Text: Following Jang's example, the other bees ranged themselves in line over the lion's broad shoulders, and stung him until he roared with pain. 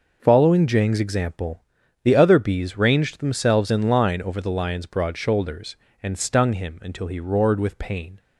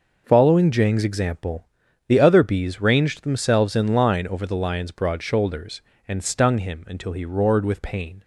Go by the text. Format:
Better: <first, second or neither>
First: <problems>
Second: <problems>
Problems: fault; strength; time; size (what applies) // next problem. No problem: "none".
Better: neither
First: none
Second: none